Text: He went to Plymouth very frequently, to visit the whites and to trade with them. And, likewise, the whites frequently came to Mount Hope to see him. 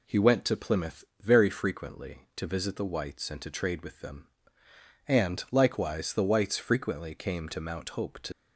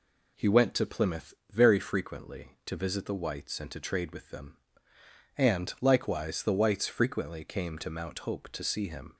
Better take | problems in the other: second | pauses between "Plymouth" and "very"; slight; at 1.0 s; 0.18 s long; slight in the second // stops before "see him"; at 8.3 s

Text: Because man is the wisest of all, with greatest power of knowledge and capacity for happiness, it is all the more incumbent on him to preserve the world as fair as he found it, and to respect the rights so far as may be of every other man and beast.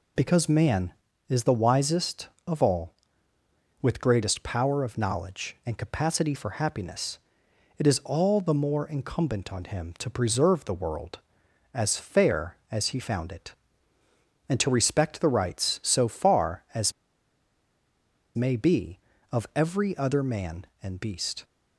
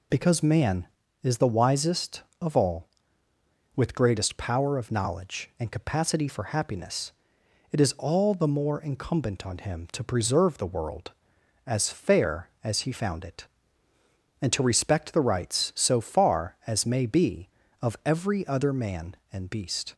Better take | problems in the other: second | pauses between "as" and "may"; strong; at 16.9 s; 1.4 s long

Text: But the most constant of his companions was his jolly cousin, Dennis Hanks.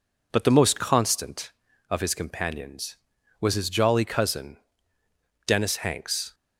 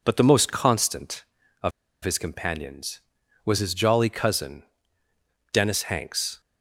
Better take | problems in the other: first | pauses between "of" and "his"; slight; at 1.7 s; 0.33 s long

